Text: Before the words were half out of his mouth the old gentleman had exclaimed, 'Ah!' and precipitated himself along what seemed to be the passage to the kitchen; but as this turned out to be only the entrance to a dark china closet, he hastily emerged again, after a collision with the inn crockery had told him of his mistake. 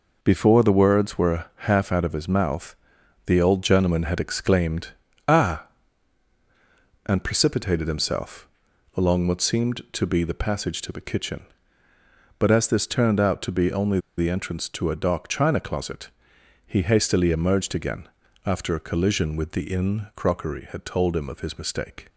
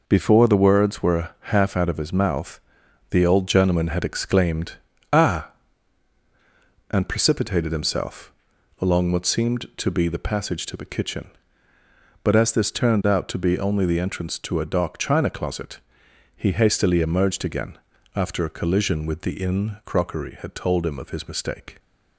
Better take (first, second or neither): second